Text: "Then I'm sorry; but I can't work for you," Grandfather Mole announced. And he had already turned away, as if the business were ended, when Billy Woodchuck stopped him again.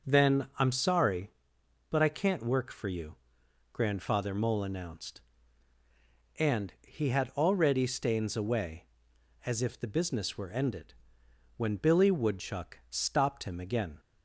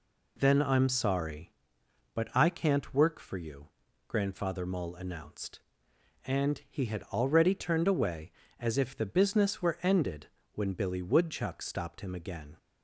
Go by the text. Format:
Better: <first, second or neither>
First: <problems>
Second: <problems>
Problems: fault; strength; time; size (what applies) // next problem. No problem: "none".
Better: second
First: starts louder than the rest; until 1.1 s; 6.5 dB // says "stains" for "turned"; at 7.8 s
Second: none